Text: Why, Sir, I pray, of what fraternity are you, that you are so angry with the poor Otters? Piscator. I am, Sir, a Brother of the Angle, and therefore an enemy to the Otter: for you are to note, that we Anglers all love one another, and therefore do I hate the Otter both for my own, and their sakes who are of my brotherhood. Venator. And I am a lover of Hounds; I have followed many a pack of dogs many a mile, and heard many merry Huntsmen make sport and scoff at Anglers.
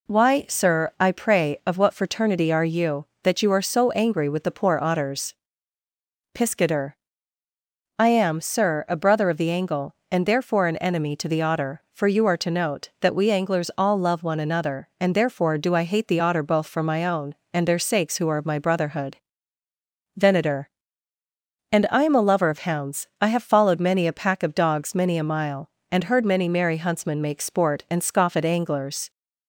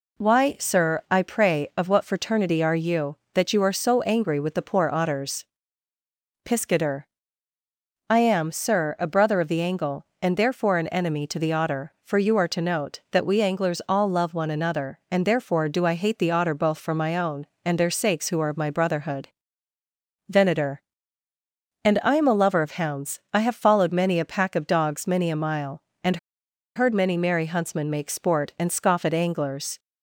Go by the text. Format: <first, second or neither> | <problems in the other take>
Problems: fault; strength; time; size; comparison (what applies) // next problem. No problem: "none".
first | pauses between "and" and "heard"; noticeable; at 26.1 s; 0.59 s long